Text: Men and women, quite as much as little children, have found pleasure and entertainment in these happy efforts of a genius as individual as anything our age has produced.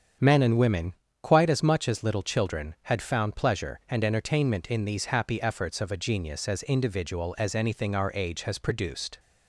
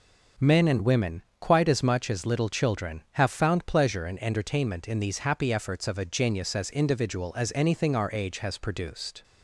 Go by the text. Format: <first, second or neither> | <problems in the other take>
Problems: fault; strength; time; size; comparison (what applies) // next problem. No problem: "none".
second | starts louder than the rest; strong; until 1.4 s; 8 dB // says "had" for "have"; at 2.8 s